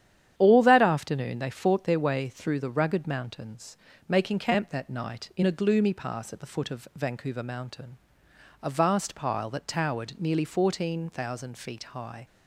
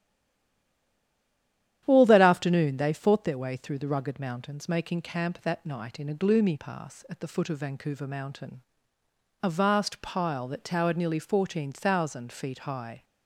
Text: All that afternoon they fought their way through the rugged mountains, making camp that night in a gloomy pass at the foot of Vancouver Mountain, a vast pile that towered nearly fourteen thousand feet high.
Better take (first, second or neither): first